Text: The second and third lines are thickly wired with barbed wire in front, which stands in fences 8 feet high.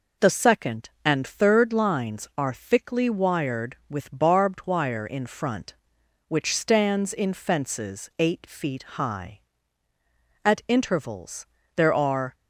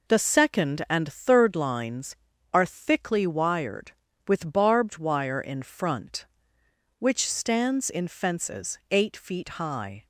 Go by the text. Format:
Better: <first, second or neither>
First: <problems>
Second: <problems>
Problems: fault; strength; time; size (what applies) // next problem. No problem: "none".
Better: second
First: goes on to say "At intervals there are"; strong; from 10.4 s on; 1.9 s long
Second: none